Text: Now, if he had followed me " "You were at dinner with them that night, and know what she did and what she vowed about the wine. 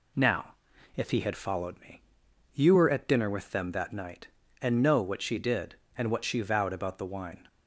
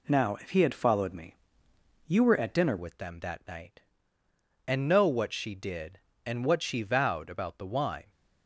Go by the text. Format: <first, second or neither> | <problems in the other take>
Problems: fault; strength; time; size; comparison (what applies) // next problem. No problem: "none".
first | changes voice at "with"; from 2.7 s on; 5.3 s long